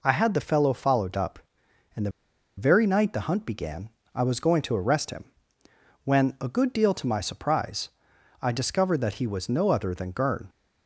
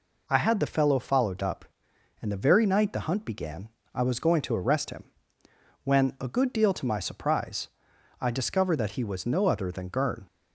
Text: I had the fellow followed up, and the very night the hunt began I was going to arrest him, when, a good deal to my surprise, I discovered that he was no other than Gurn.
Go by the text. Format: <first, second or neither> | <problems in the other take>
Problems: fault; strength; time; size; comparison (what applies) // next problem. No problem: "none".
second | pauses between "the" and "very"; noticeable; at 2.1 s; 0.46 s long // pauses between "began" and "I"; slight; at 3.8 s; 0.26 s long; slight in the second